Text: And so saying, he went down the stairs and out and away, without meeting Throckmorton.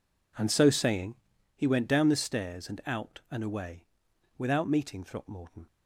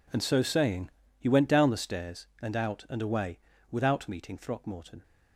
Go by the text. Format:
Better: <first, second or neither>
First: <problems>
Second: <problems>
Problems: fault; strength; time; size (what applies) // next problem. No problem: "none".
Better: neither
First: none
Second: none